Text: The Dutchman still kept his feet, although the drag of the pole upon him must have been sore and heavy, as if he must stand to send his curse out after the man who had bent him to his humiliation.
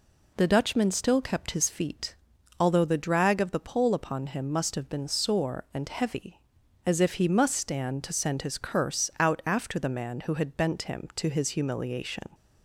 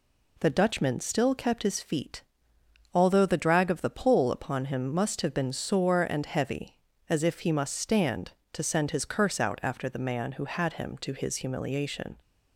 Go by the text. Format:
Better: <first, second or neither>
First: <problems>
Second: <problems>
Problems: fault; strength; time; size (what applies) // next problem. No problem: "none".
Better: first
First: none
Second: skips "bent"; at 10.7 s